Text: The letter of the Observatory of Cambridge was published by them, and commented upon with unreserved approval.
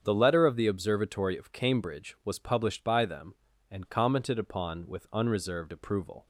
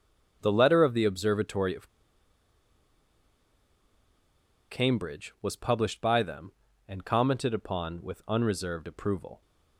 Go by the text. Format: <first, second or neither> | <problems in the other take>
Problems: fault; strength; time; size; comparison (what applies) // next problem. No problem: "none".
first | starts louder than the rest; strong; until 1.4 s; 8 dB; strong in the first // pauses between "of" and "Cambridge"; strong; at 1.8 s; 2.8 s long